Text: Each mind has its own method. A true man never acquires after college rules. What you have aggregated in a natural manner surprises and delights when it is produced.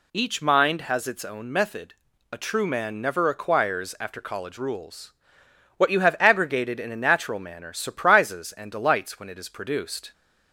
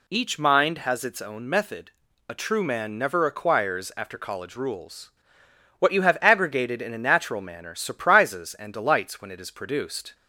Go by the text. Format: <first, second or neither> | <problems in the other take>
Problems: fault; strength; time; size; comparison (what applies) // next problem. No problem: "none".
neither | none